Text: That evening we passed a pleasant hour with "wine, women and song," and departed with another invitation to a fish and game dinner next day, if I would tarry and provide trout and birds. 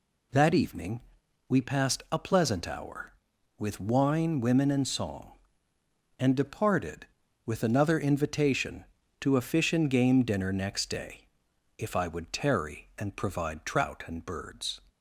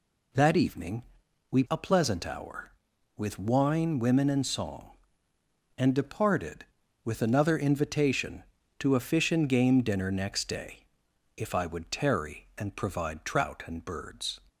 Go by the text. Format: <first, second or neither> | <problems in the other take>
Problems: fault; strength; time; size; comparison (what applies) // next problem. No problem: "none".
first | pauses between "evening" and "we"; noticeable; at 1.0 s; 0.48 s long; noticeable in the first // skips "passed"; at 1.6 s